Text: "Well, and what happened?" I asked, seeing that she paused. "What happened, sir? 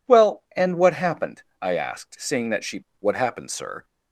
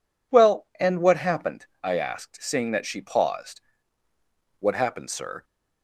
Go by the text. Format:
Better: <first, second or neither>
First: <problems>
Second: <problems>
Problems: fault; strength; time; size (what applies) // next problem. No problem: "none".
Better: second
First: skips "paused"; at 2.9 s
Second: none